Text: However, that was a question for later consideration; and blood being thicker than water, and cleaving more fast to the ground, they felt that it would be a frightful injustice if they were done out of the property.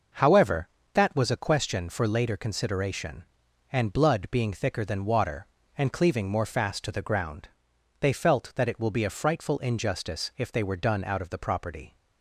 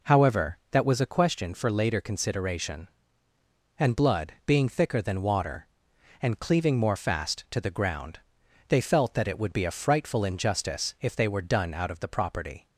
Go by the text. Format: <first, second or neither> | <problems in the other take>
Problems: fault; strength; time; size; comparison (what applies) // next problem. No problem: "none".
second | says "will" for "would"; at 8.7 s